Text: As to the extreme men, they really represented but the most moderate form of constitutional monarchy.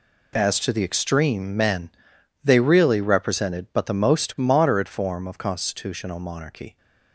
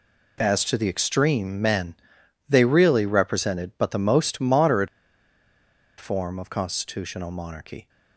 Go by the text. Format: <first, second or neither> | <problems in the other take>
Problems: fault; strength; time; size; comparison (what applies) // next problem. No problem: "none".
first | pauses between "moderate" and "form"; at 4.8 s; 1.1 s long